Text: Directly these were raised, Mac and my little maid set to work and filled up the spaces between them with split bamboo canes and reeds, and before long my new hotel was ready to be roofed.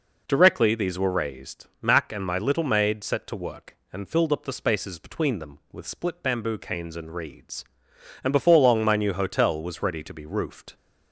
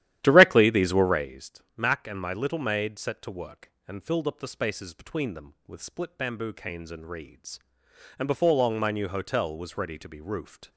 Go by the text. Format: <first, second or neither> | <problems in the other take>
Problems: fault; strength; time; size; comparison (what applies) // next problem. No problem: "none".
first | starts louder than the rest; strong; until 1.4 s; 12.5 dB